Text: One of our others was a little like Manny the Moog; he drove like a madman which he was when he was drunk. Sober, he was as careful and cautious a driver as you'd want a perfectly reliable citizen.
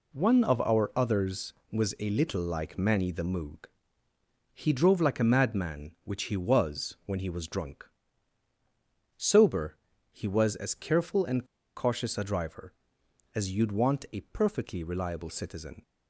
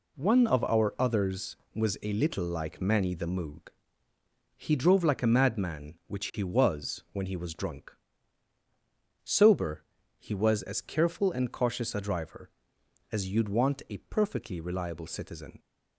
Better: second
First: pauses between "and" and "cautious"; slight; at 11.4 s; 0.30 s long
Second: none

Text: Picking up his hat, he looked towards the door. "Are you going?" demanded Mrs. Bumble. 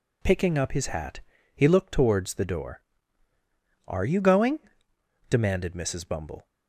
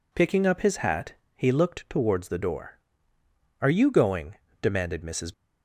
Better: first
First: none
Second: stops before "Bumble"; at 5.3 s

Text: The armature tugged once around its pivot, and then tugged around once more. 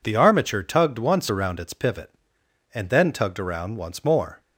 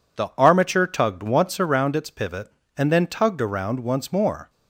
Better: neither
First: none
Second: none

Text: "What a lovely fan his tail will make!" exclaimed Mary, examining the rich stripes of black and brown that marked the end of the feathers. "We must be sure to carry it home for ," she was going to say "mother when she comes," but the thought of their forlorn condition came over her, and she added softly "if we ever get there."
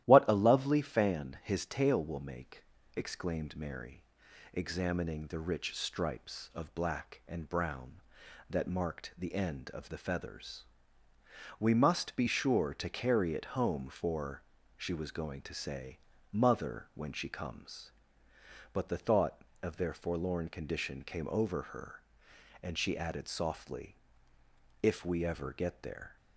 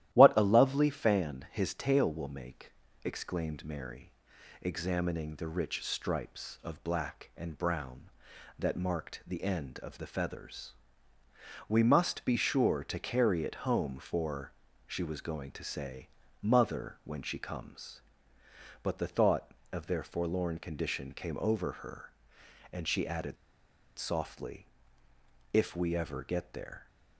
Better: first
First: starts louder than the rest; strong; until 1.0 s; 13 dB // pauses between "say" and "mother"; slight; at 15.9 s; 0.34 s long // pauses between "softly" and "if"; noticeable; at 23.9 s; 0.84 s long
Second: starts louder than the rest; strong; until 1.1 s; 13 dB // pauses between "say" and "mother"; slight; at 16.0 s; 0.34 s long // pauses between "added" and "softly"; noticeable; at 23.3 s; 0.63 s long // pauses between "softly" and "if"; noticeable; at 24.6 s; 0.84 s long

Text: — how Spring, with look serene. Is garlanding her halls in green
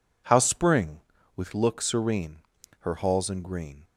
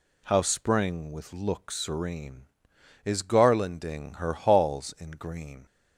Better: second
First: skips "Is garlanding"; at 2.5 s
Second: none

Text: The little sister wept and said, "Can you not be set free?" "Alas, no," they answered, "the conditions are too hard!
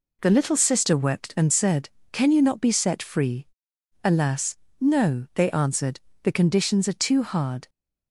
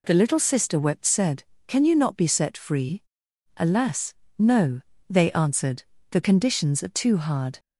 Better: first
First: none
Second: skips "and"; at 1.0 s

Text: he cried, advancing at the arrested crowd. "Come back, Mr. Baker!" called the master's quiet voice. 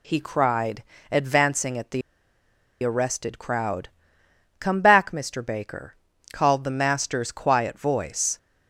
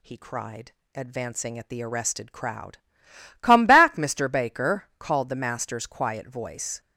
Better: second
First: pauses between "the" and "arrested"; noticeable; at 2.0 s; 0.82 s long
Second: none

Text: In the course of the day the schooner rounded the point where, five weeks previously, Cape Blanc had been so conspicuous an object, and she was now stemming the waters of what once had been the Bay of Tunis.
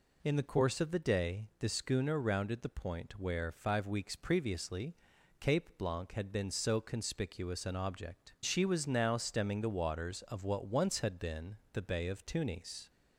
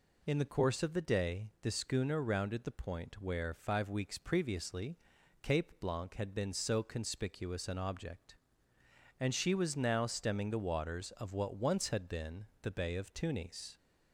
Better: second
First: skips "and"; at 8.3 s // pauses between "been" and "the"; slight; at 11.5 s; 0.18 s long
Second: pauses between "been" and "the"; slight; at 12.4 s; 0.18 s long

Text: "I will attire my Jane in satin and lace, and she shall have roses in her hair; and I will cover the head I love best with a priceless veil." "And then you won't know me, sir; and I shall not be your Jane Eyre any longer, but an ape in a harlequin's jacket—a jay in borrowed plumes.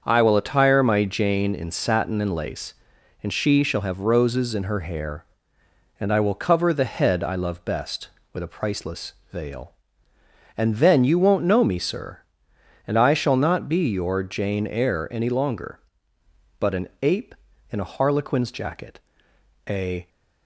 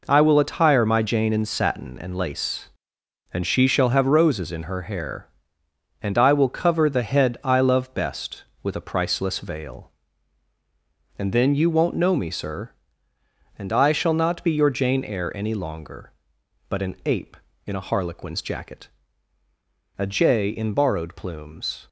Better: second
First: starts louder than the rest; until 1.0 s; 7 dB // pauses between "priceless" and "veil"; slight; at 9.1 s; 0.18 s long // stops before "jay in borrowed plumes"; at 20.0 s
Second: none

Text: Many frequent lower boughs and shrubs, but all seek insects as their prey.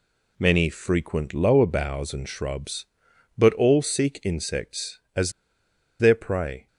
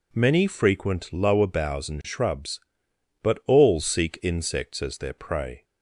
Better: second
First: pauses between "as" and "their"; noticeable; at 5.3 s; 0.68 s long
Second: none

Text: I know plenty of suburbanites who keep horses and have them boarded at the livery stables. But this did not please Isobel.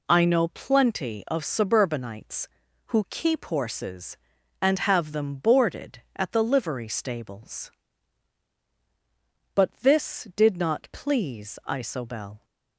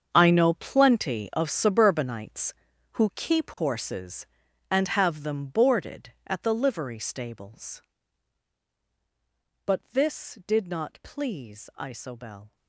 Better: first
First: none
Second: gets quieter; strong; throughout; 14 dB

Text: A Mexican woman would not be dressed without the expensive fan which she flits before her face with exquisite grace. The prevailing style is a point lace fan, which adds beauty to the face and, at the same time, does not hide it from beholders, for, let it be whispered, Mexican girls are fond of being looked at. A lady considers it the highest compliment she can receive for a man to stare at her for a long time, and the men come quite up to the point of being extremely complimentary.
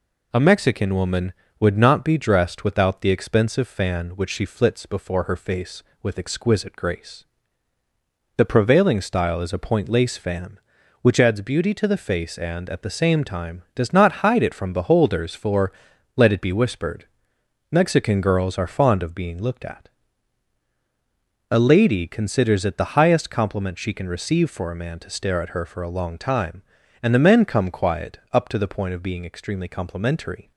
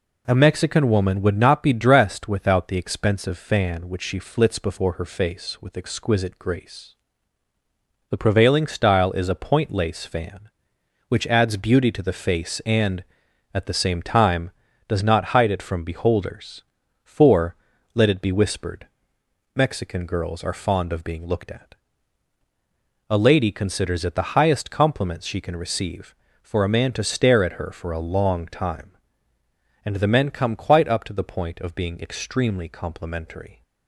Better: second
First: says "quiet" for "quite"; at 27.7 s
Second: none

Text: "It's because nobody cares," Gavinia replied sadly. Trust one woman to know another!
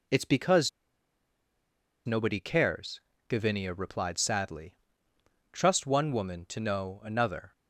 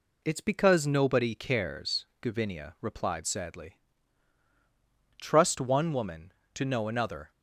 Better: second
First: pauses between "because" and "nobody"; strong; at 0.6 s; 1.3 s long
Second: none

